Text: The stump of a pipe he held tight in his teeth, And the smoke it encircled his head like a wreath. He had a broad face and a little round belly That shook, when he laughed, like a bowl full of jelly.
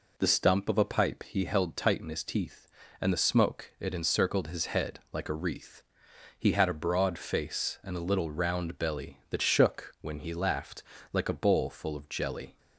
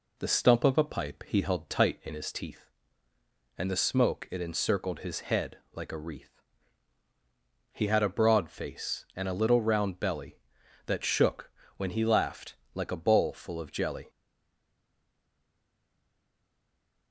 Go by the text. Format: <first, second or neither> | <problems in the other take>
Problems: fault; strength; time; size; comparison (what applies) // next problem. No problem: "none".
first | pauses between "head" and "like"; slight; at 5.5 s; 0.16 s long // stays silent after the last word; strong; from 14.0 s on; 3.1 s long